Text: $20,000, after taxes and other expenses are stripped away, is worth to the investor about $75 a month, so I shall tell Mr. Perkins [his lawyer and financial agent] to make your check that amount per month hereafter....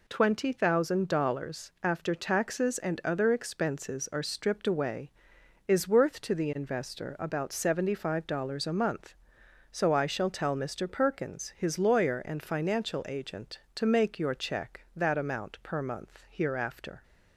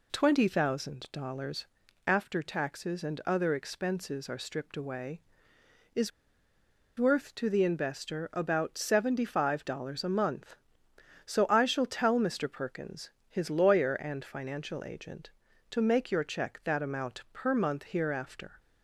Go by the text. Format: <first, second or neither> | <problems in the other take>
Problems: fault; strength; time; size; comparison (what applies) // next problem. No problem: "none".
first | pauses between "is" and "worth"; noticeable; at 6.1 s; 0.87 s long // pauses between "Perkins" and "his"; slight; at 13.1 s; 0.18 s long